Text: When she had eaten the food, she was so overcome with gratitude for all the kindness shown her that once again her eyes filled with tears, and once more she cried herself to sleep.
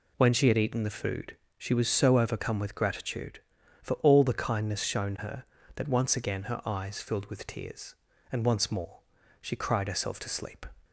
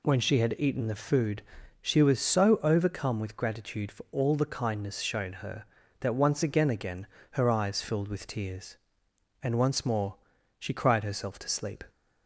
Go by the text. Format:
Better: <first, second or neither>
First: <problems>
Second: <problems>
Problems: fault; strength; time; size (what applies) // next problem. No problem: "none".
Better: first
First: pauses between "more" and "she"; at 9.0 s; 0.40 s long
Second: says "again" twice; at 6.7 s // pauses between "more" and "she"; at 10.1 s; 0.44 s long